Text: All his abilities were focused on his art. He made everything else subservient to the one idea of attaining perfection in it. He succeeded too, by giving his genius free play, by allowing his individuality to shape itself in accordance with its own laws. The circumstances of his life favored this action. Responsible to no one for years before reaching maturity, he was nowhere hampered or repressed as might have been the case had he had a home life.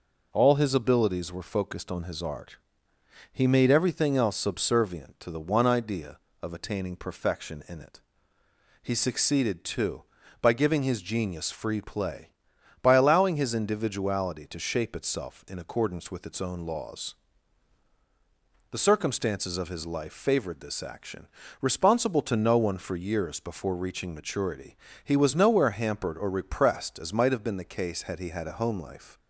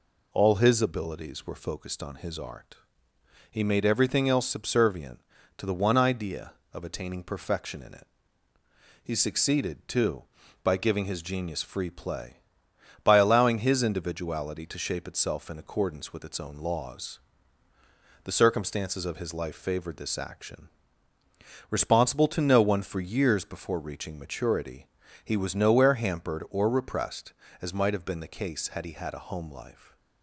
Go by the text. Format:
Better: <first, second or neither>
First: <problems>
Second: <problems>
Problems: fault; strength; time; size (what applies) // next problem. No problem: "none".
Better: neither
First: none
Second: none